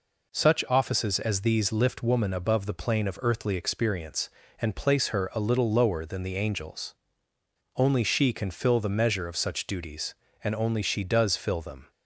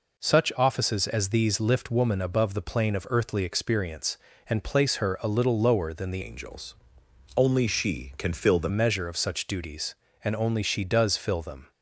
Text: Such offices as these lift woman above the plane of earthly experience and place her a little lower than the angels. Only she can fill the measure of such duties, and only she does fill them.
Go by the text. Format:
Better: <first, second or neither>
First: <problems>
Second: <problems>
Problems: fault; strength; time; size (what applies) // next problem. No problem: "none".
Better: first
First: none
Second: changes voice from "angels" to "the"; from 6.2 to 8.6 s; 2.4 s long